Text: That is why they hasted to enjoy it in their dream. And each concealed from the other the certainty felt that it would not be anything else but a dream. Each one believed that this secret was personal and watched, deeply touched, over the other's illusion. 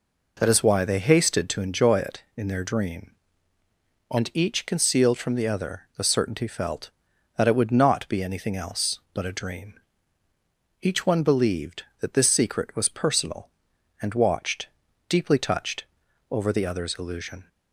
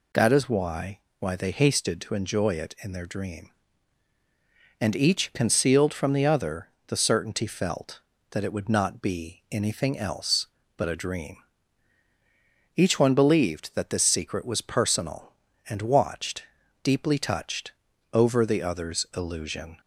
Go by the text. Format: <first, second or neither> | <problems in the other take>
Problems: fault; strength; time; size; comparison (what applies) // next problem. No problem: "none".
first | says "why" twice; at 1.1 s // pauses between "other" and "the"; slight; at 6.6 s; 0.18 s long